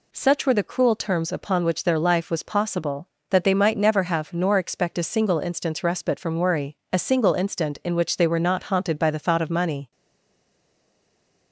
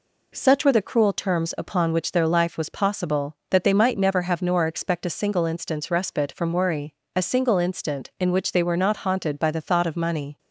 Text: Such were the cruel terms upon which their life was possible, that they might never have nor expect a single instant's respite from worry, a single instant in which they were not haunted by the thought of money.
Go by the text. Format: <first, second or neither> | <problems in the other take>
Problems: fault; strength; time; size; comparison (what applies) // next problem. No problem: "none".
second | stays silent after the last word; noticeable; from 9.9 s on; 1.6 s long